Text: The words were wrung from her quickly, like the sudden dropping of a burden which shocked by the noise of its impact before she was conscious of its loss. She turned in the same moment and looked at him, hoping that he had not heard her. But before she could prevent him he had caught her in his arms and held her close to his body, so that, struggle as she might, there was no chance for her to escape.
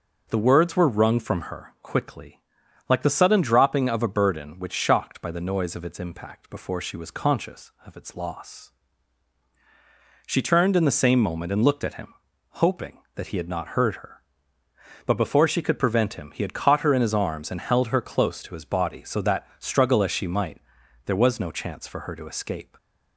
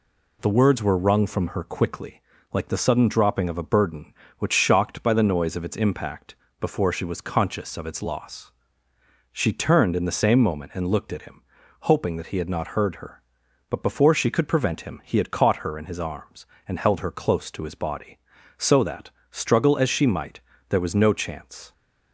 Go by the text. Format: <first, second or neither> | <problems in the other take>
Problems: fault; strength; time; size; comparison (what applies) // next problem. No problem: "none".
first | pauses between "impact" and "before"; slight; at 6.3 s; 0.26 s long // stops before "for her to escape"; at 21.7 s